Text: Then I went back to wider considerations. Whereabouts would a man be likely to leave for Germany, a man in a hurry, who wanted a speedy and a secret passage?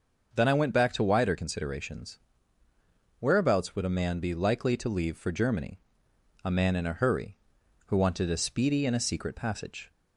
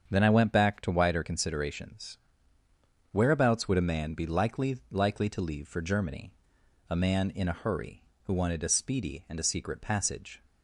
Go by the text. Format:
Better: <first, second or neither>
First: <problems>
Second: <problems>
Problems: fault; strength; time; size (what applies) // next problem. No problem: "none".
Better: first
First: starts louder than the rest; until 1.3 s; 6.5 dB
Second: starts louder than the rest; strong; until 1.1 s; 7 dB // says "likely" twice; at 4.9 s